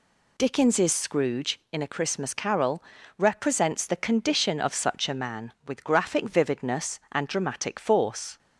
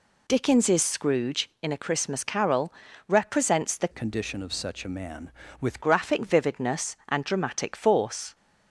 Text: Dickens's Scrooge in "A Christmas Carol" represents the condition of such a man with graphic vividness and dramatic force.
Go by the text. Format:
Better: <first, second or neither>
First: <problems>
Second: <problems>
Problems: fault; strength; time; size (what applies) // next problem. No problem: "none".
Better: first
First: pauses between "Carol" and "represents"; slight; at 2.8 s; 0.36 s long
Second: pauses between "Carol" and "represents"; slight; at 2.7 s; 0.36 s long // changes voice from "condition" to "with"; from 3.9 to 5.8 s; 1.9 s long